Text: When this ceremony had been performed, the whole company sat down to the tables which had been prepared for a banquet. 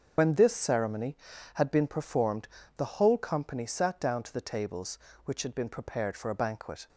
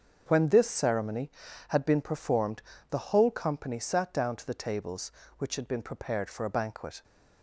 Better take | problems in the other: second | loses the start of "When"; at 0.1 s; 40 ms // starts louder than the rest; strong; until 1.5 s; 7.5 dB; also in the second

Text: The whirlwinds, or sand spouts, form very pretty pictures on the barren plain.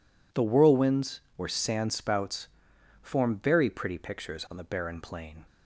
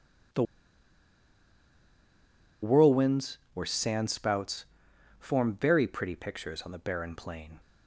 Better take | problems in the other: first | pauses between "The" and "whirlwinds"; strong; at 0.4 s; 2.1 s long

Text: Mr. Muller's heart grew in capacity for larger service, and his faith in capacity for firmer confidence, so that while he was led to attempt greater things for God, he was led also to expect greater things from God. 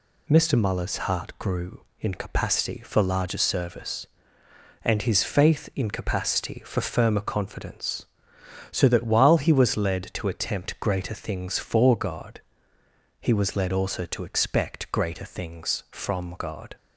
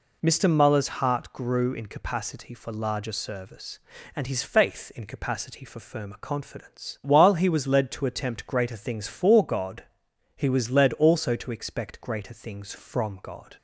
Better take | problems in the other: first | skips "so that"; at 7.0 s

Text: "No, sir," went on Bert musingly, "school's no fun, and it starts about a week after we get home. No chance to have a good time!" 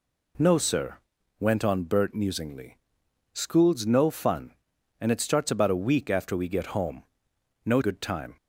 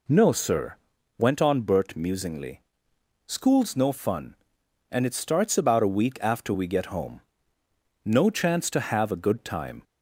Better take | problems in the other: second | skips "chance to have a"; at 7.8 s

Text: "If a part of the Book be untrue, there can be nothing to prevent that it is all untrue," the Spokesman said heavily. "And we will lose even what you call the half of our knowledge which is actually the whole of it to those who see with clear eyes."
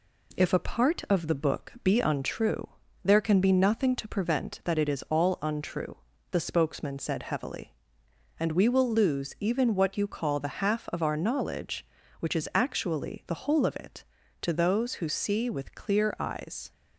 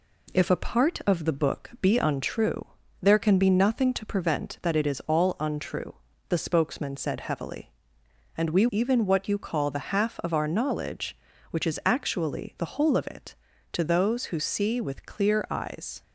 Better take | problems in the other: first | skips "will lose"; at 8.6 s

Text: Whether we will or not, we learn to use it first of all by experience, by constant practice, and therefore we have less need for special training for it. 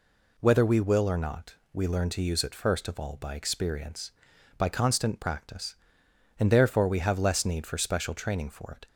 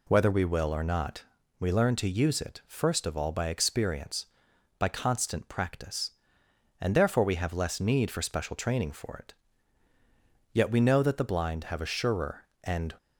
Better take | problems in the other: first | goes on to say "Yet we know that the blind have a surer and"; strong; from 10.5 s on; 2.4 s long

